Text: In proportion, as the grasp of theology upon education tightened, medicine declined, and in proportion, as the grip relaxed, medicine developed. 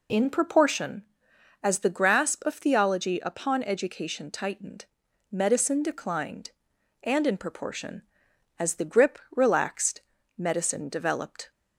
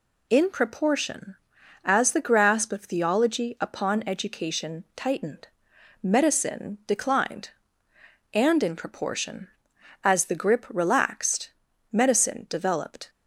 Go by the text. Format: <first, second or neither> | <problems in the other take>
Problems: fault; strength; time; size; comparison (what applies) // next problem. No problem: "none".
neither | none